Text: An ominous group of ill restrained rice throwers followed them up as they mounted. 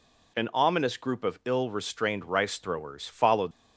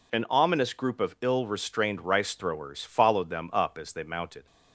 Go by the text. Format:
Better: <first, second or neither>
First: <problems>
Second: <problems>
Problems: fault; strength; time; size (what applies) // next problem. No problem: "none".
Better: second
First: stops before "them up as they mounted"; at 3.5 s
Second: none